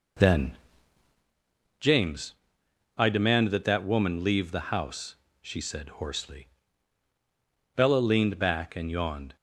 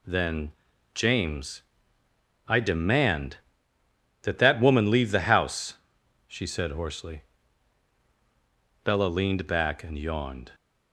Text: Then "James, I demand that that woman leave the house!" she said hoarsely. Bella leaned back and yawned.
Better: second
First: starts louder than the rest; noticeable; until 1.3 s; 4 dB // pauses between "Then" and "James"; at 0.5 s; 1.2 s long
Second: pauses between "Then" and "James"; at 0.5 s; 0.42 s long

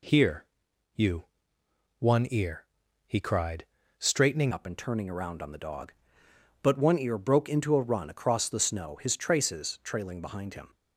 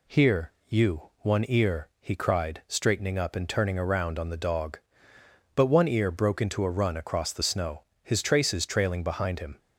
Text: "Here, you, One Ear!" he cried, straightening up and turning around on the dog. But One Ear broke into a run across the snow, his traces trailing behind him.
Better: second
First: changes voice at "up"; from 4.5 s on; 6.2 s long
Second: none

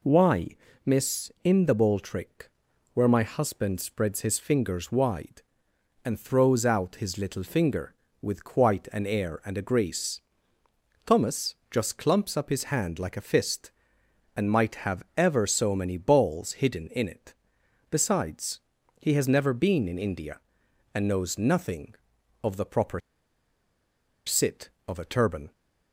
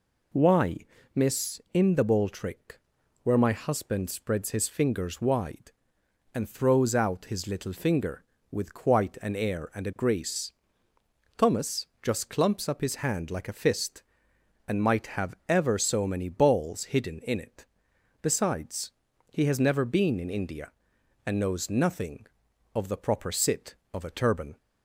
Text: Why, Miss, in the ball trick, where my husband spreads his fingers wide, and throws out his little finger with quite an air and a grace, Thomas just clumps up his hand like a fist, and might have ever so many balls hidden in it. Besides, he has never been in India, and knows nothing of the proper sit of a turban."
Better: second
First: pauses between "Thomas" and "just"; slight; at 11.5 s; 0.16 s long // pauses between "proper" and "sit"; strong; at 22.9 s; 1.2 s long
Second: pauses between "Thomas" and "just"; slight; at 11.8 s; 0.16 s long

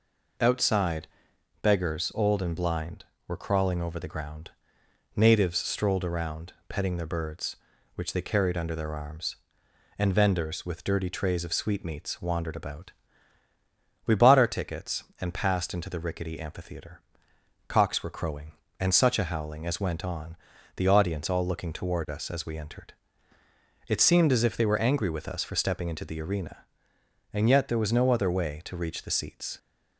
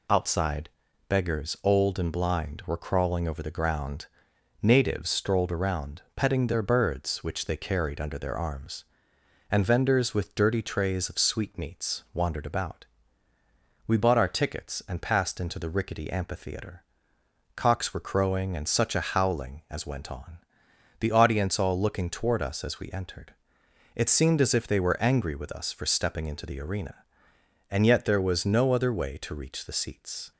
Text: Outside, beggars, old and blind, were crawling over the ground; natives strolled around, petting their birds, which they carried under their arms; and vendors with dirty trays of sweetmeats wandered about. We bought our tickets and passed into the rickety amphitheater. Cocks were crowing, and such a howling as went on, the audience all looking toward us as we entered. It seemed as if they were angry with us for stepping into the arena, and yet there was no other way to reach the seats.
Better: neither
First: none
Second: none

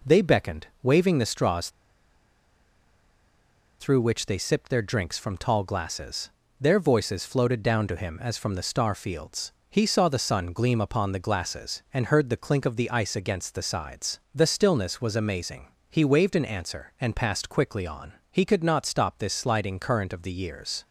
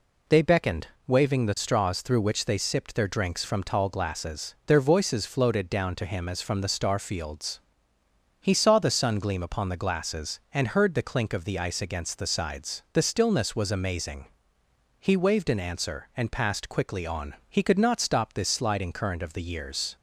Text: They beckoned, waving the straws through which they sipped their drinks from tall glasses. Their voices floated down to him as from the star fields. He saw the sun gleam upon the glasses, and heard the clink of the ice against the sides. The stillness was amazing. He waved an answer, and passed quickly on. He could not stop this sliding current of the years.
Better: second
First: pauses between "straws" and "through"; strong; at 1.6 s; 2.1 s long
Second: none

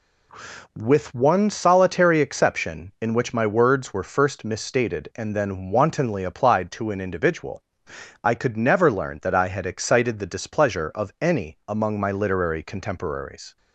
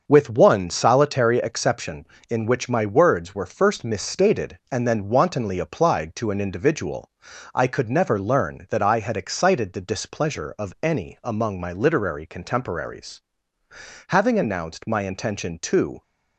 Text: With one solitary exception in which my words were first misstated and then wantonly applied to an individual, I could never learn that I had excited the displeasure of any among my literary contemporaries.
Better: first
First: none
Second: starts louder than the rest; until 1.0 s; 6.5 dB // goes on to say "Having announced my intention to"; strong; from 14.0 s on; 1.9 s long

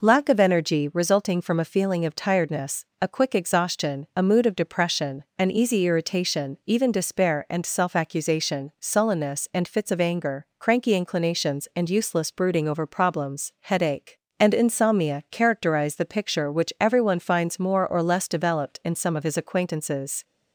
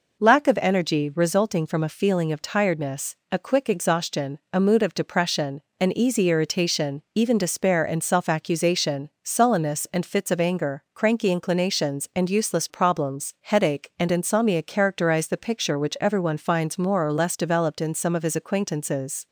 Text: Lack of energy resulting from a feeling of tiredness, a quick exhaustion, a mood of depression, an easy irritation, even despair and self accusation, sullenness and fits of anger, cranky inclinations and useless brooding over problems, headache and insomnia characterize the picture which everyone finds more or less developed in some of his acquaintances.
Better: first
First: none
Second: skips "brooding over"; at 12.6 s

